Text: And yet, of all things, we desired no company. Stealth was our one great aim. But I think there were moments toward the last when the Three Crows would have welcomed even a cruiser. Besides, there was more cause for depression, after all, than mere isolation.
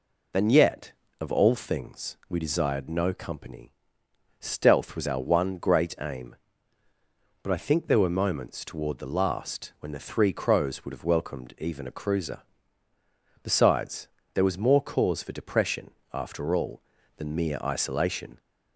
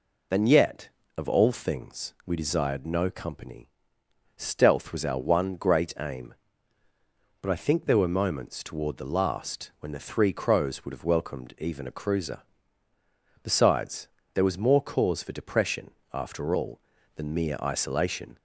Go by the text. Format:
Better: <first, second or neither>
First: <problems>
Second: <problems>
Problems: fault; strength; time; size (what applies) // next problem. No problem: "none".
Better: neither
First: none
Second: none